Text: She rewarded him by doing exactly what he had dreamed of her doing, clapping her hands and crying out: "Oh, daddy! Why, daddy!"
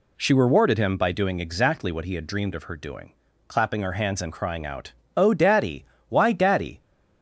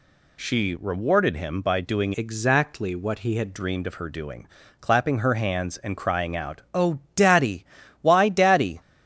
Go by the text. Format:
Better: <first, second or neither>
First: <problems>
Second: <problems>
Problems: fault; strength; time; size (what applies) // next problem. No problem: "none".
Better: first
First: none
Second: changes voice from "exactly" to "had"; from 2.1 to 3.5 s; 1.4 s long